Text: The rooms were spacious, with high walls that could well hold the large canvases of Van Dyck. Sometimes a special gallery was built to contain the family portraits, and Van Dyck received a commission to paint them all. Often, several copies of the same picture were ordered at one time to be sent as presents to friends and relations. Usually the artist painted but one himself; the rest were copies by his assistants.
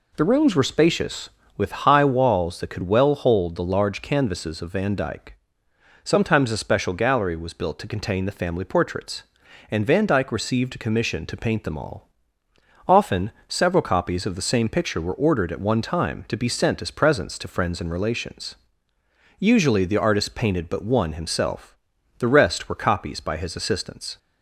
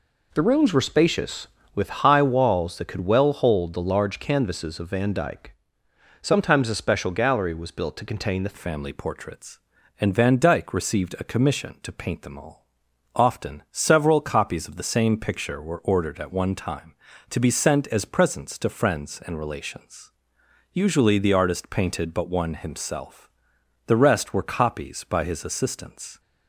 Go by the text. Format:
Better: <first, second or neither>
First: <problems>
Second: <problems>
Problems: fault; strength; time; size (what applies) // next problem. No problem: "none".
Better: first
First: none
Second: changes voice at "family"; from 8.5 s on; 17.6 s long